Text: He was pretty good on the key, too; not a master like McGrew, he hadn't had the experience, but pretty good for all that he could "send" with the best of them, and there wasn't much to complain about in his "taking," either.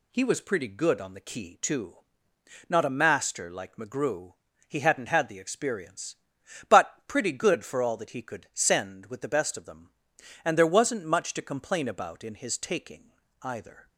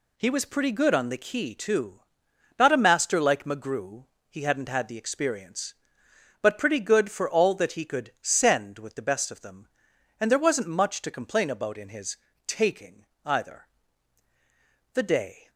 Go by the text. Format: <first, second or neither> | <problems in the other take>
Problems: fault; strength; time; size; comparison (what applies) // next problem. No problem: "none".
first | pauses between "his" and "taking"; slight; at 12.1 s; 0.32 s long // goes on to say "The day"; from 14.9 s on; 0.56 s long